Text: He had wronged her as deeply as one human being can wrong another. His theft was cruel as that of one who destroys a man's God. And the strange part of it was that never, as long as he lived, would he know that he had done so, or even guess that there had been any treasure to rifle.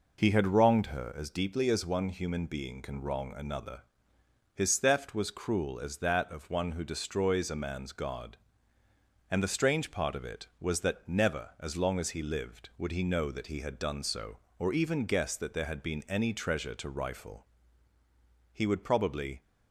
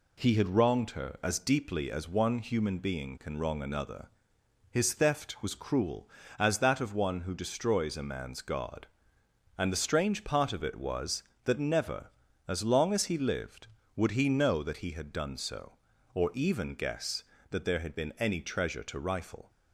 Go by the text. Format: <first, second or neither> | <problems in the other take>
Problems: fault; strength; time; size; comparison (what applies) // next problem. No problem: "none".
second | goes on to say "He would probably"; noticeable; from 18.5 s on; 0.92 s long